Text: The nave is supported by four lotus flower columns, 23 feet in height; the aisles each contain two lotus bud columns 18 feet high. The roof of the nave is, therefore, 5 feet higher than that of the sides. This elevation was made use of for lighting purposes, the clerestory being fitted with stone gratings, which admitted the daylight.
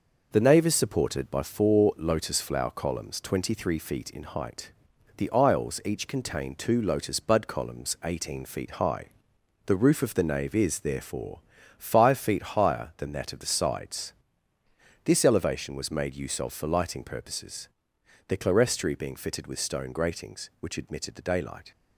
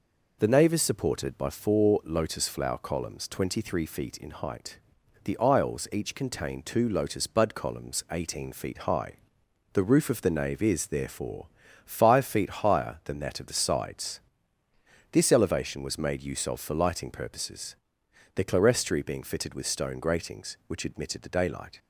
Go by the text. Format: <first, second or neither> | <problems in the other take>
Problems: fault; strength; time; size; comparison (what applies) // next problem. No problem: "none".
second | gets quieter; noticeable; throughout; 5 dB